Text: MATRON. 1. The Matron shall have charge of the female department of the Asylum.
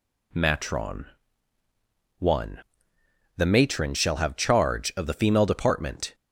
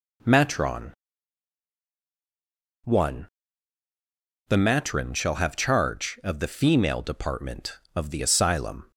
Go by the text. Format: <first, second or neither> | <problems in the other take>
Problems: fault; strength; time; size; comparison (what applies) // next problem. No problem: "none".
second | stops before "of the Asylum"; at 6.1 s